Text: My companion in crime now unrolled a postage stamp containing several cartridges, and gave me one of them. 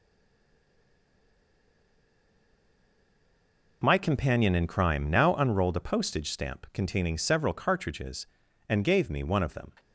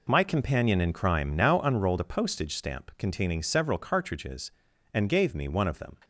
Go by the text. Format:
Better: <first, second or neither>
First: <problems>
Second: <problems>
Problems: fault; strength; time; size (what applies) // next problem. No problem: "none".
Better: second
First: stays silent before the first word; strong; until 3.8 s; 3.8 s long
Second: none